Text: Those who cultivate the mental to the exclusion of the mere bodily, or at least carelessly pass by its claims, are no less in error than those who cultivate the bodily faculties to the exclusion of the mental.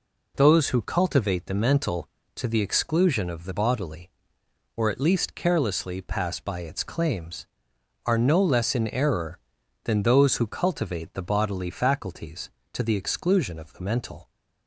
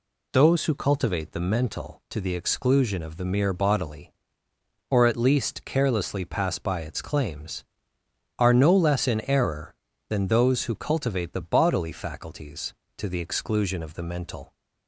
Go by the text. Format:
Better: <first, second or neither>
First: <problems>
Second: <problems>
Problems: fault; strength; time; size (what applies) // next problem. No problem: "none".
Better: second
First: skips "mere"; at 3.5 s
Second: none